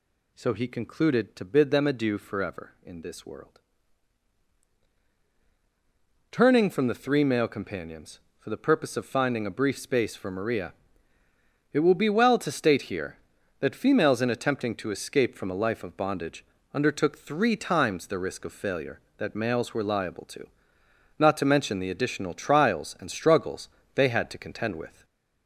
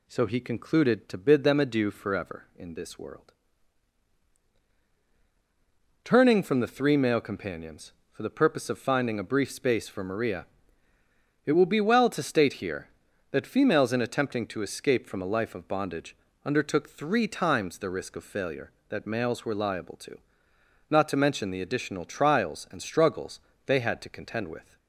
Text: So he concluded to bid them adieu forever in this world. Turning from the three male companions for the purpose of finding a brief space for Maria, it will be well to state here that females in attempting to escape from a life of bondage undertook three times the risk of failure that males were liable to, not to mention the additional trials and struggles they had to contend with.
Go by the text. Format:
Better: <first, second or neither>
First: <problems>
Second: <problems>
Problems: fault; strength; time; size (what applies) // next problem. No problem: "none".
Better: second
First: gets louder; throughout; 4 dB // pauses between "bondage" and "undertook"; slight; at 16.4 s; 0.30 s long // pauses between "struggles" and "they"; slight; at 23.6 s; 0.26 s long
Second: pauses between "bondage" and "undertook"; slight; at 16.1 s; 0.30 s long // pauses between "struggles" and "they"; slight; at 23.3 s; 0.26 s long